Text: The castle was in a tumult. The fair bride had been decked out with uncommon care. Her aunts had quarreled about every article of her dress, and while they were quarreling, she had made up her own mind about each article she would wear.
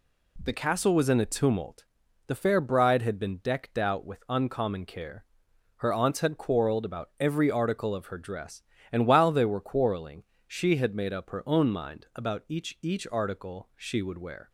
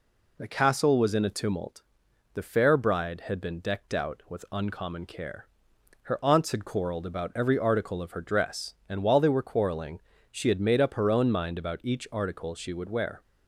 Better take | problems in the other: second | says "each" twice; at 12.8 s

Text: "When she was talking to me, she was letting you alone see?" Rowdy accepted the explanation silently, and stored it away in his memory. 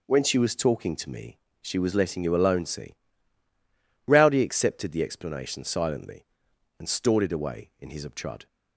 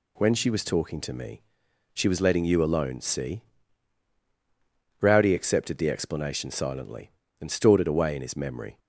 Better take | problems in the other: second | says "obtrud" for "memory"; at 8.0 s

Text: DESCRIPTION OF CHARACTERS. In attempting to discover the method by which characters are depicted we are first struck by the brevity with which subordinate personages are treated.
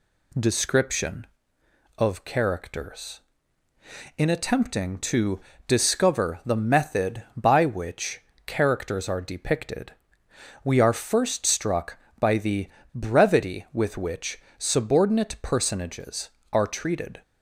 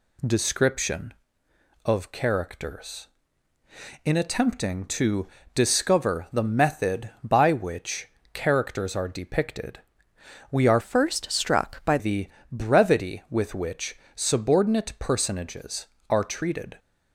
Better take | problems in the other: first | pauses between "to" and "discover"; slight; at 5.2 s; 0.28 s long; slight in the first // pauses between "which" and "characters"; slight; at 8.0 s; 0.26 s long; slight in the first // pauses between "depicted" and "we"; noticeable; at 9.7 s; 0.72 s long; noticeable in the first // changes voice from "first" to "by"; from 10.8 to 11.9 s; 1.1 s long // pauses between "the" and "brevity"; slight; at 12.2 s; 0.24 s long; slight in the first // pauses between "which" and "subordinate"; slight; at 13.9 s; 0.18 s long; slight in the first

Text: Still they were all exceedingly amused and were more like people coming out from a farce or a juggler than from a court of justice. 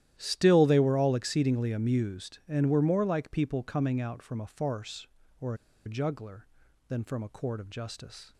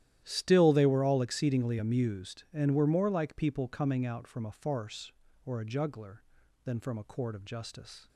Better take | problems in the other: second | starts louder than the rest; strong; until 1.1 s; 12.5 dB; strong in the second // pauses between "or" and "a"; slight; at 5.5 s; 0.31 s long

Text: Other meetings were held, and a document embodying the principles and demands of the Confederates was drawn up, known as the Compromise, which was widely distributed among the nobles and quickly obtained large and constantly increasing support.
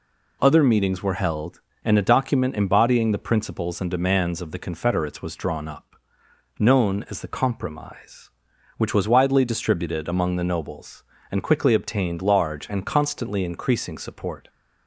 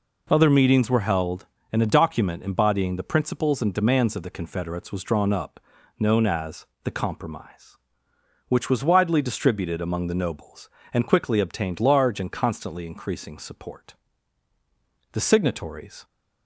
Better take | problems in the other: first | pauses between "as" and "the"; slight; at 6.6 s; 0.18 s long // goes on to say "The signatories"; noticeable; from 15.1 s on; 0.92 s long

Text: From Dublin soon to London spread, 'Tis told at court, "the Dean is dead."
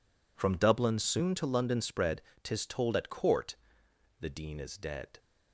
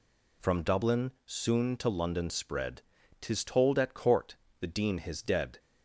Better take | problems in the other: first | pauses between "Dublin" and "soon"; slight; at 1.1 s; 0.16 s long // says "his" for "is"; at 4.9 s

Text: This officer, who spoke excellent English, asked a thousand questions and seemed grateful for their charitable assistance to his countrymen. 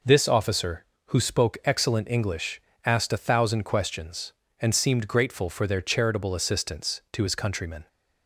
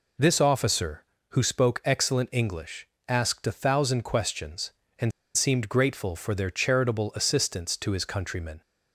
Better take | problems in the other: first | pauses between "and" and "seemed"; slight; at 5.1 s; 0.23 s long

